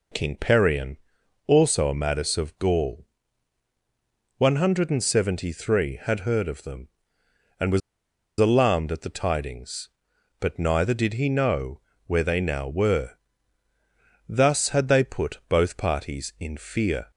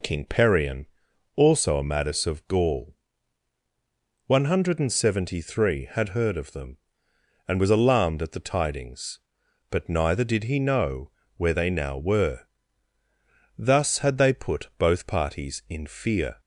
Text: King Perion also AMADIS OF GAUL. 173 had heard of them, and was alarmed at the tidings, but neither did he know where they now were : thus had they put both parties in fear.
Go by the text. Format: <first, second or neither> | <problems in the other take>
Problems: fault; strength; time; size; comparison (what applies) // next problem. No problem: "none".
second | pauses between "Perion" and "also"; noticeable; at 0.9 s; 0.48 s long; noticeable in the second // pauses between "was" and "alarmed"; noticeable; at 7.8 s; 0.60 s long // pauses between "know" and "where"; slight; at 11.8 s; 0.26 s long; slight in the second